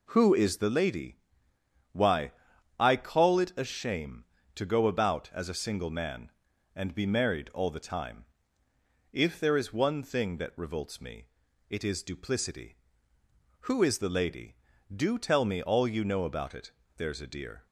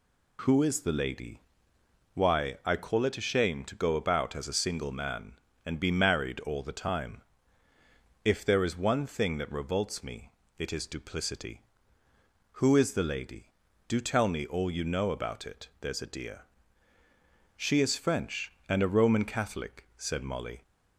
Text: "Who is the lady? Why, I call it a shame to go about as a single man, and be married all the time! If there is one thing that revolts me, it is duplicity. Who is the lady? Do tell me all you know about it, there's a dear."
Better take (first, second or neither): first